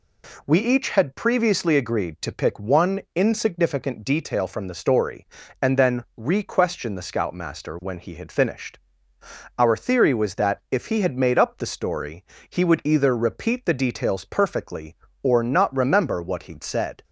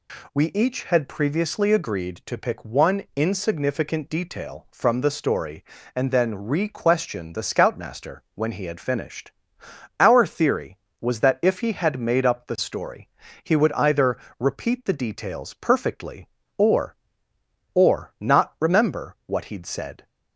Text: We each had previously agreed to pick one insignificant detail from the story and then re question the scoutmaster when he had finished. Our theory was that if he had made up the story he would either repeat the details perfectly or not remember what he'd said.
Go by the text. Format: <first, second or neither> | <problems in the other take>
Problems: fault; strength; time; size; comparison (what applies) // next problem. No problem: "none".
first | pauses between "story" and "he"; slight; at 13.0 s; 0.34 s long; slight in the first // pauses between "either" and "repeat"; slight; at 14.1 s; 0.18 s long // says "or" twice; at 17.7 s